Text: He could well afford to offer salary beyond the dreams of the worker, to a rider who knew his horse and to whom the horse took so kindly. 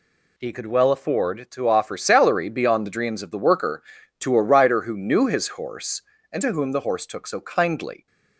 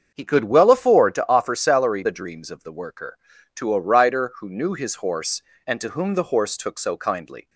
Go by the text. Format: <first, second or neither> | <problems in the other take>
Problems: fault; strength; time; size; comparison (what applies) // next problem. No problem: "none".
first | starts louder than the rest; until 1.1 s; 7 dB // skips "beyond"; at 2.0 s